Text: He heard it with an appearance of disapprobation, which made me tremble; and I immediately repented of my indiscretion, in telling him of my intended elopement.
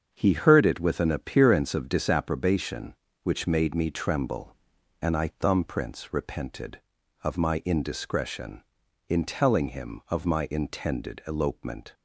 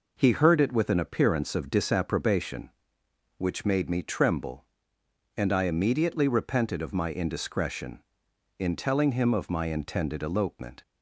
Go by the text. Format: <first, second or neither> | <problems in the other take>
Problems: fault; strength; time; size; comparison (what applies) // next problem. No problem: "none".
second | starts louder than the rest; until 1.1 s; 7 dB // says "thumbprints" for "immediately"; at 5.2 s